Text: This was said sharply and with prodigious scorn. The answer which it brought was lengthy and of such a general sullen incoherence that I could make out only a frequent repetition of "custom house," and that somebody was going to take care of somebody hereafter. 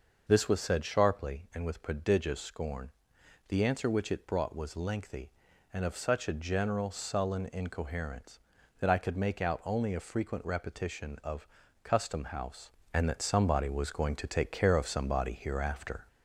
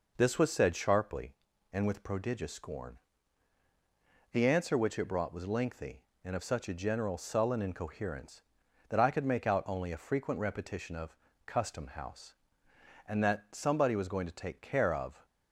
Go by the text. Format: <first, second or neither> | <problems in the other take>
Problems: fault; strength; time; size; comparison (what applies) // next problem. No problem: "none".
first | pauses between "of" and "custom"; slight; at 11.1 s; 0.30 s long; slight in the first // stops before "somebody hereafter"; at 15.2 s